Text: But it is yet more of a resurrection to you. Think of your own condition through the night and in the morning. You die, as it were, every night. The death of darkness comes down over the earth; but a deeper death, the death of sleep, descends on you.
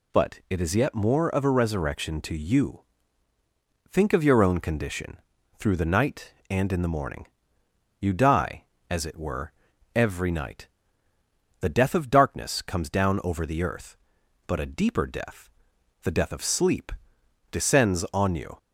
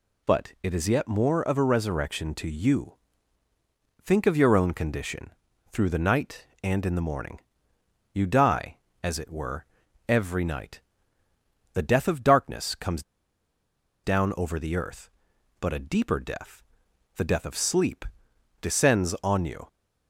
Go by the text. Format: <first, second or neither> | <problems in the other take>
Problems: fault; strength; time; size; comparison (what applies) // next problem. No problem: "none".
first | pauses between "condition" and "through"; at 5.3 s; 0.40 s long; also in the first // pauses between "comes" and "down"; at 13.0 s; 1.0 s long